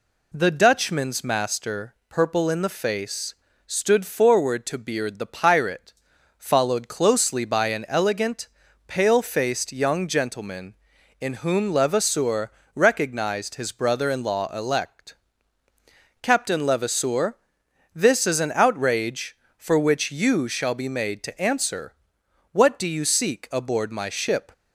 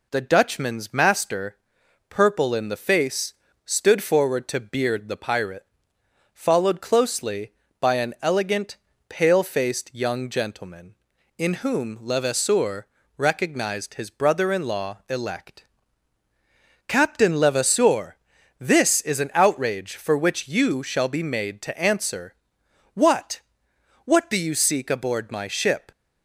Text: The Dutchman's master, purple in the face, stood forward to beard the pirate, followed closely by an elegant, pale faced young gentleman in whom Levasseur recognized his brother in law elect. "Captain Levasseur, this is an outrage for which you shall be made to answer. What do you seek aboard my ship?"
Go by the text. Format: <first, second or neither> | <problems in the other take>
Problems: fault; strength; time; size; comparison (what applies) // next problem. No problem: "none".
first | pauses between "Levasseur" and "recognized"; slight; at 12.8 s; 0.30 s long; slight in the first // says "What" twice; at 24.0 s